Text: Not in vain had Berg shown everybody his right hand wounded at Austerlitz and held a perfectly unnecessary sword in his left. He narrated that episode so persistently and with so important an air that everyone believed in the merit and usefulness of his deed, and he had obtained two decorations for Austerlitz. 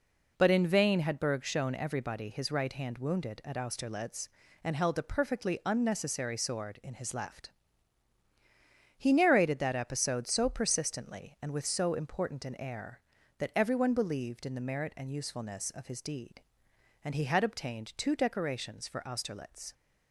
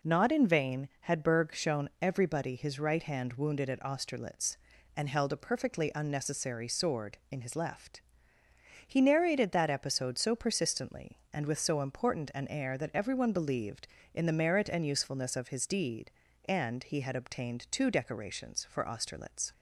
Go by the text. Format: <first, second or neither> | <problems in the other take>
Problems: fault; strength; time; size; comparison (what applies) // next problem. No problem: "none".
second | says "But" for "Not"; at 0.3 s